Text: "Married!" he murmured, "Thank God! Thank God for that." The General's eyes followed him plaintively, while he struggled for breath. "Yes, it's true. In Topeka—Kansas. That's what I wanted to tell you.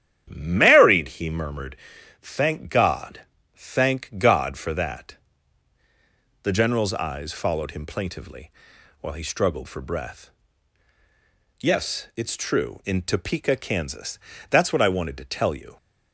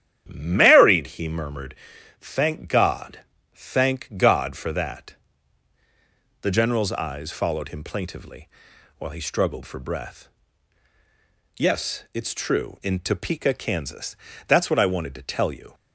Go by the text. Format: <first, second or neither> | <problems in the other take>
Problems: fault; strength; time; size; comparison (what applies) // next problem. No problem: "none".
neither | starts louder than the rest; strong; the same in both